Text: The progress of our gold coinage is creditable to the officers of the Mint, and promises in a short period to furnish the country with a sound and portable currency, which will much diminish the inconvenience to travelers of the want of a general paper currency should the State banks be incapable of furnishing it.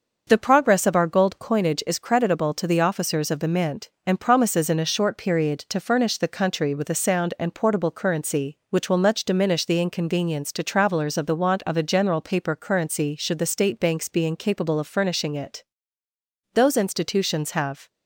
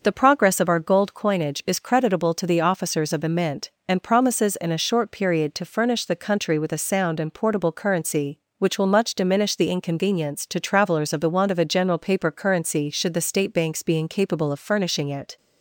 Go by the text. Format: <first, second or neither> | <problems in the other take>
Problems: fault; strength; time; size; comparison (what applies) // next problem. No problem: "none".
second | starts louder than the rest; until 1.2 s; 6.5 dB; noticeable in the second // goes on to say "Those institutions have"; from 16.5 s on; 1.3 s long